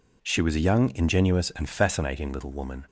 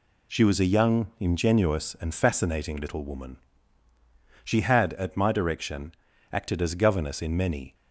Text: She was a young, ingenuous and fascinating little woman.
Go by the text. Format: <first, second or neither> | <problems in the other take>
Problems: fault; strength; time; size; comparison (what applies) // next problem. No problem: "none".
first | goes on to say "She had at my direction acted as governess in many"; strong; from 4.4 s on; 3.3 s long